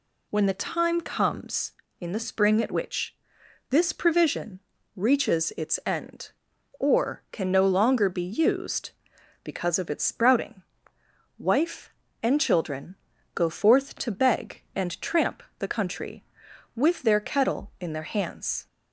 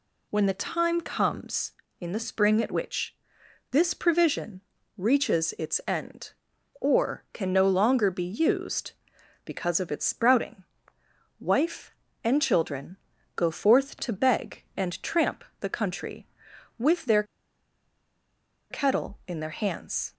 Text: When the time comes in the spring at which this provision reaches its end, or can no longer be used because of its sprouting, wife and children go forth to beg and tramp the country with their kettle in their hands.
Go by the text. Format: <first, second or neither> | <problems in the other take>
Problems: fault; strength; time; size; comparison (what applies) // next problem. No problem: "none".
first | pauses between "which" and "this"; noticeable; at 3.1 s; 0.56 s long; noticeable in the first // pauses between "provision" and "reaches"; slight; at 4.6 s; 0.34 s long; slight in the first // pauses between "children" and "go"; at 12.9 s; 0.38 s long; also in the first // pauses between "tramp" and "the"; slight; at 15.4 s; 0.18 s long; slight in the first // pauses between "their" and "kettle"; strong; at 17.2 s; 1.4 s long